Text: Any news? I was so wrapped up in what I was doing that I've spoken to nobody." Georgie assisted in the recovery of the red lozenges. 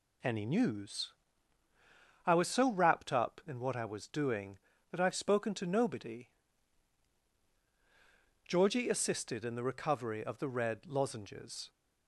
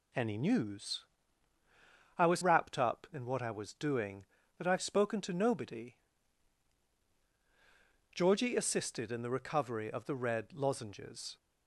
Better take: first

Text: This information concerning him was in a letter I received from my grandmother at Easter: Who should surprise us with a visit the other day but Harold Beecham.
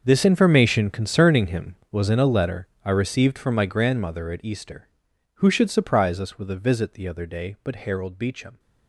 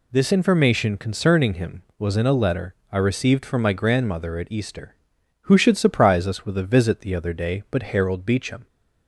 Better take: second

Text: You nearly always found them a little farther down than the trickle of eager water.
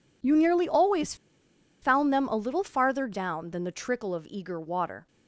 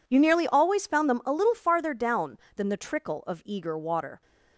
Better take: second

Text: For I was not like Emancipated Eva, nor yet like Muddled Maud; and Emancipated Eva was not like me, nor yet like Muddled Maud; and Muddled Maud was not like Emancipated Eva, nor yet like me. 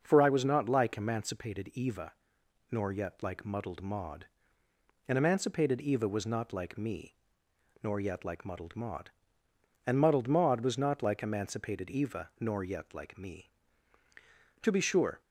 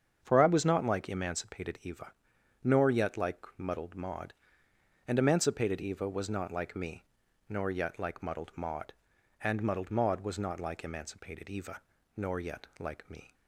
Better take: second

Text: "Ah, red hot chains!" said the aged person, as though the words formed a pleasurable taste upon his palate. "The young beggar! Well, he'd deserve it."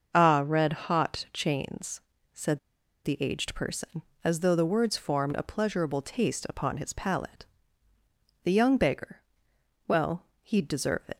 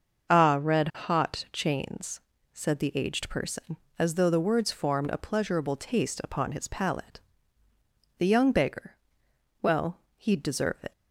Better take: second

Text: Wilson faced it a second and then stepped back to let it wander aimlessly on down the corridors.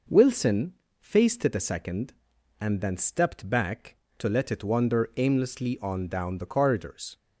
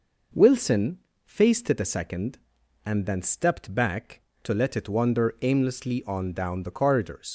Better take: first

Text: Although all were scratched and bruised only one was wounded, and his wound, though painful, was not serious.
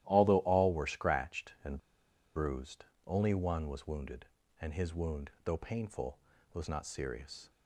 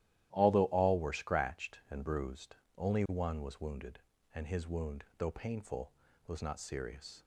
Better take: second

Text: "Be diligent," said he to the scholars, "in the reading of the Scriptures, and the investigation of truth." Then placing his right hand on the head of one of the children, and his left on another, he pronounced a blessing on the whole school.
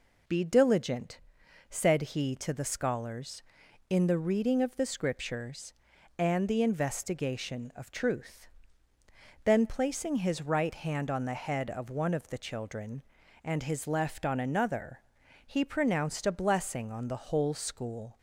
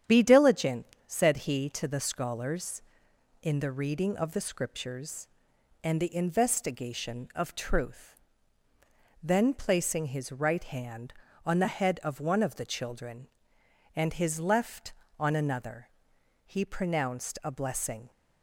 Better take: first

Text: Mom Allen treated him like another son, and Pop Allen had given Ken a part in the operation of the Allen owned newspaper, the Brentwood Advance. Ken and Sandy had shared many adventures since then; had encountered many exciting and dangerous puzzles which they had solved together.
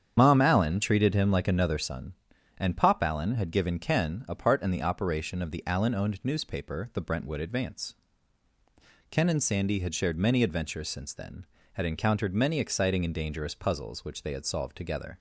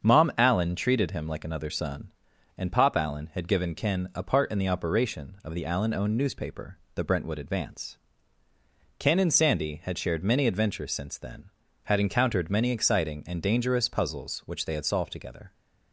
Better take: second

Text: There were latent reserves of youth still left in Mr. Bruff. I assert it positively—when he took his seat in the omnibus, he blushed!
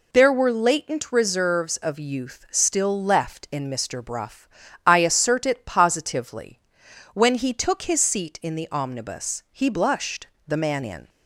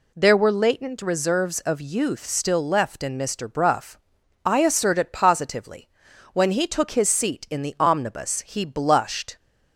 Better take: second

